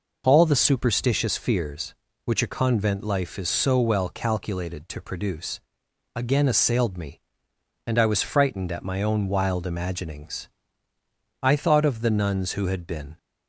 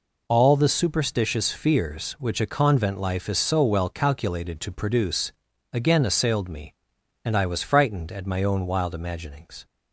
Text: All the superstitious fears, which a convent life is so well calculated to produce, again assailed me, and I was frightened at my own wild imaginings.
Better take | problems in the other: second | goes on to say "I thought of the nuns who had been"; strong; from 11.4 s on; 1.7 s long

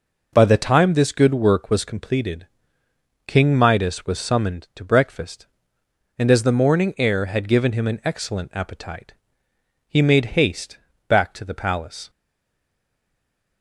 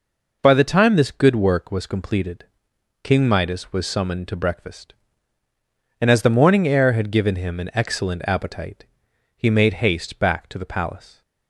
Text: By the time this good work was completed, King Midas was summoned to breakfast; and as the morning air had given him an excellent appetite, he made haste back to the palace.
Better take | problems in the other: second | pauses between "haste" and "back"; slight; at 10.7 s; 0.30 s long // stays silent after the last word; noticeable; from 12.0 s on; 1.6 s long

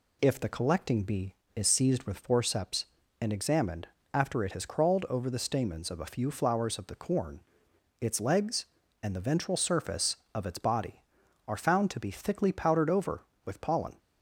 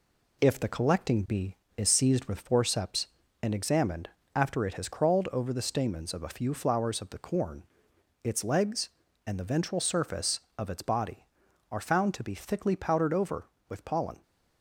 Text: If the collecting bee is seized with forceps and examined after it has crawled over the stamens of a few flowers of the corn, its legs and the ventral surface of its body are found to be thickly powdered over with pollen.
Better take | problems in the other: first | gets quieter; noticeable; throughout; 4.5 dB // pauses between "examined" and "after"; slight; at 4.0 s; 0.26 s long; slight in the first

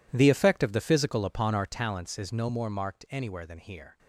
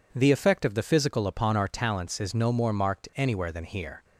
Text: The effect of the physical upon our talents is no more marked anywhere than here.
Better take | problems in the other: second | gets quieter; strong; throughout; 17.5 dB

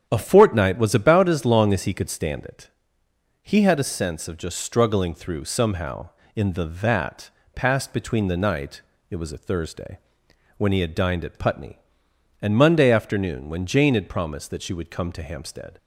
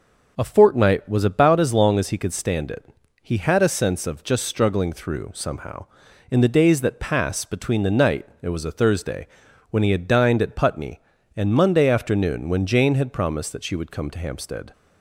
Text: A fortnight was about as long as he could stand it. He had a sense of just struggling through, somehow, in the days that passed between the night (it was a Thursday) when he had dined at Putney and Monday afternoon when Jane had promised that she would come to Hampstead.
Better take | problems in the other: second | starts louder than the rest; strong; until 1.1 s; 8.5 dB // skips "days"; at 6.6 s // pauses between "that" and "passed"; slight; at 7.2 s; 0.26 s long

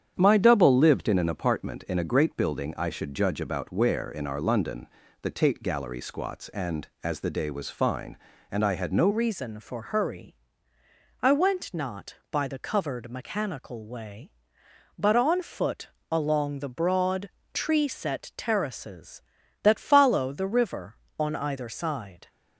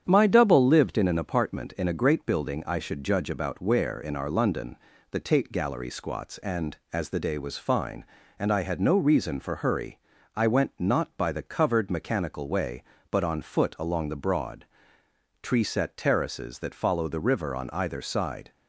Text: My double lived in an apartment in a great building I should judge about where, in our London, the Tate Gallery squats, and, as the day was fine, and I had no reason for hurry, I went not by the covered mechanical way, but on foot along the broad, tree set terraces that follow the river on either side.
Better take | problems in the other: second | starts louder than the rest; strong; until 1.1 s; 8.5 dB; strong in the second // changes voice at "reason"; from 9.0 s on; 13.2 s long // pauses between "foot" and "along"; slight; at 15.8 s; 0.22 s long

